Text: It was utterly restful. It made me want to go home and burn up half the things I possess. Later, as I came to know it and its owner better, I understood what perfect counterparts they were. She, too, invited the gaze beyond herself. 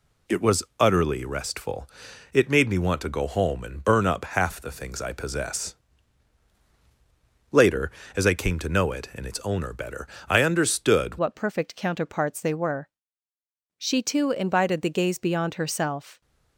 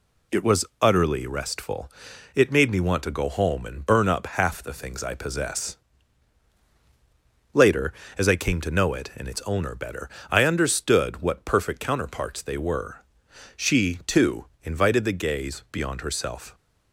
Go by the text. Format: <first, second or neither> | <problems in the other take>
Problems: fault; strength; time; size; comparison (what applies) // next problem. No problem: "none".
second | pauses between "was" and "utterly"; slight; at 0.6 s; 0.16 s long; slight in the second // changes voice at "what"; from 11.1 s on; 5.1 s long